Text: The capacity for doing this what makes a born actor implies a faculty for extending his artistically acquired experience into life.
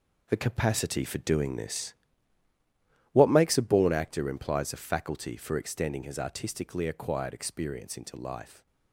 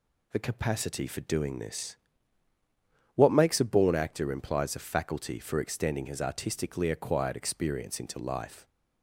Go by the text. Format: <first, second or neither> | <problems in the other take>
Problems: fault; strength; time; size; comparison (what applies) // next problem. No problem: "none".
second | gets quieter; strong; throughout; 9.5 dB // pauses between "this" and "what"; at 1.9 s; 1.1 s long; also in the second